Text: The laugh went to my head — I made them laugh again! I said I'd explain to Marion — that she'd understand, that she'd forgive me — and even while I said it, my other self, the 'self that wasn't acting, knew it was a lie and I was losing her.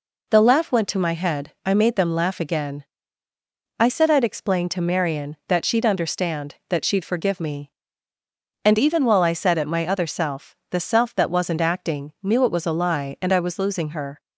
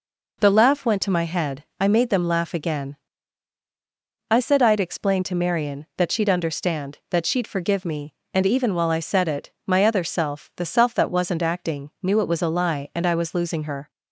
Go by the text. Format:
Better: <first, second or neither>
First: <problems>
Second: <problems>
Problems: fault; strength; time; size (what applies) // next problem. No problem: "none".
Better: neither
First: none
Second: none